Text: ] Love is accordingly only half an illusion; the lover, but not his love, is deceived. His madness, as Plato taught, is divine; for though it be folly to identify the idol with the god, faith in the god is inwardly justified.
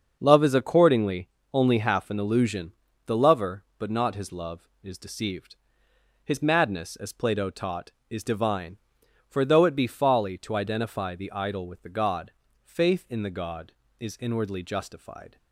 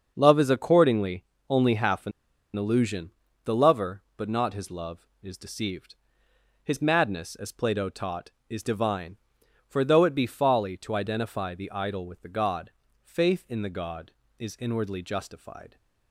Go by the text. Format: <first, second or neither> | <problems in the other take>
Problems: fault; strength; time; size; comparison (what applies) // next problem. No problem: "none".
first | starts louder than the rest; until 1.1 s; 6.5 dB; also in the first // pauses between "accordingly" and "only"; slight; at 1.2 s; 0.24 s long; slight in the first // pauses between "an" and "illusion"; at 2.1 s; 0.44 s long